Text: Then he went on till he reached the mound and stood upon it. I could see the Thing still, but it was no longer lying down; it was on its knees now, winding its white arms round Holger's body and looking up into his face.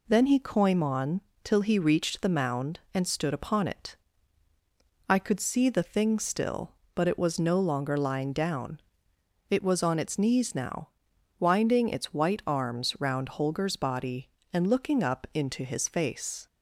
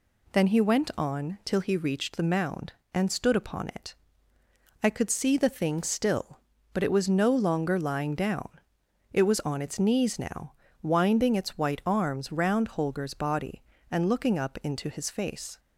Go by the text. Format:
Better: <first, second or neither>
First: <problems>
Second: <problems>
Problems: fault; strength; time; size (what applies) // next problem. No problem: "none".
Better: second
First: says "coim" for "went"; at 0.3 s // pauses between "on" and "till"; slight; at 1.2 s; 0.22 s long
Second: none